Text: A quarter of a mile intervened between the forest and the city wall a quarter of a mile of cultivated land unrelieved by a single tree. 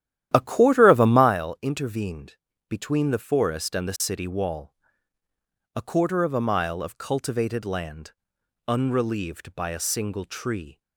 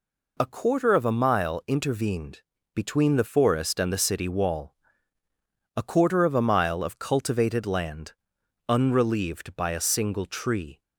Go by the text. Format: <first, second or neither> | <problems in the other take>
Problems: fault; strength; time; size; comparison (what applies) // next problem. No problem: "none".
second | starts louder than the rest; strong; until 1.3 s; 11.5 dB // pauses between "intervened" and "between"; slight; at 2.3 s; 0.32 s long; slight in the second // pauses between "wall" and "a"; at 4.7 s; 1.0 s long; also in the second // pauses between "land" and "unrelieved"; noticeable; at 8.1 s; 0.56 s long; noticeable in the second